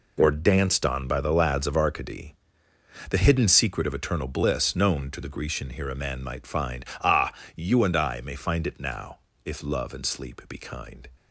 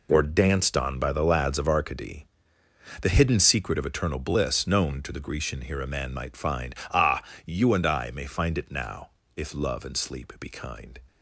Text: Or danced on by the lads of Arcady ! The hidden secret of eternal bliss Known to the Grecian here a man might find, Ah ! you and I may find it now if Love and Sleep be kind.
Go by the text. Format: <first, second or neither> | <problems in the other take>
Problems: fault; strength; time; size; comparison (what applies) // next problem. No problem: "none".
neither | pauses between "now" and "if"; slight; the same in both